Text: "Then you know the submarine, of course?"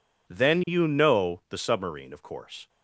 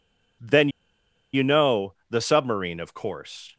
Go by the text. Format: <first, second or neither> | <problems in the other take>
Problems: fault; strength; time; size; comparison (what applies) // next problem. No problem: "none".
first | pauses between "Then" and "you"; noticeable; at 0.6 s; 0.64 s long // pauses between "know" and "the"; slight; at 1.9 s; 0.16 s long